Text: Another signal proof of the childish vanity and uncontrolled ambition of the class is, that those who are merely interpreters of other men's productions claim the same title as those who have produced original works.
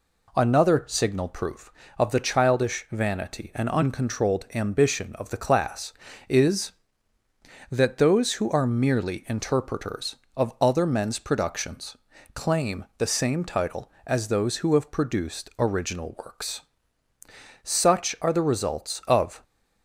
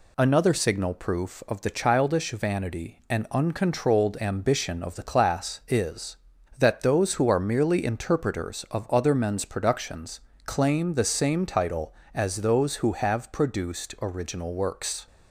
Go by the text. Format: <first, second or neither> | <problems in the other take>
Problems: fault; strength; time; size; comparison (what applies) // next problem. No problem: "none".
second | pauses between "productions" and "claim"; slight; at 11.9 s; 0.36 s long; slight in the second // goes on to say "Such are the results of"; strong; from 17.6 s on; 1.8 s long